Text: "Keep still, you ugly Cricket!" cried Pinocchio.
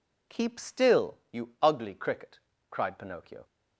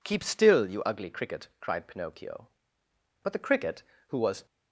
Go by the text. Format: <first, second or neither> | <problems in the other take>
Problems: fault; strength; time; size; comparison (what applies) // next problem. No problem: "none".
first | goes on to say "But the Cricket who was"; noticeable; from 3.2 s on; 1.2 s long